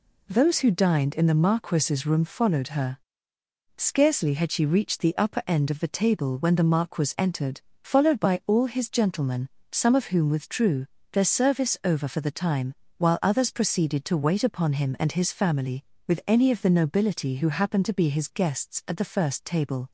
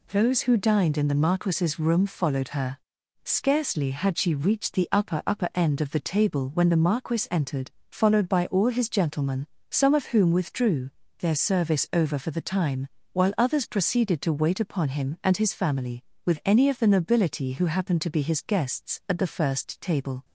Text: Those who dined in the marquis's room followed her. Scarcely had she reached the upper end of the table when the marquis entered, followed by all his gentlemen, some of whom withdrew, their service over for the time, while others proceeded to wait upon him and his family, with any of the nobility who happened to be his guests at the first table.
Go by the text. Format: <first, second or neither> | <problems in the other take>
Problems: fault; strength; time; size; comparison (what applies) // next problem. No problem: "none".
first | says "upper" twice; at 5.2 s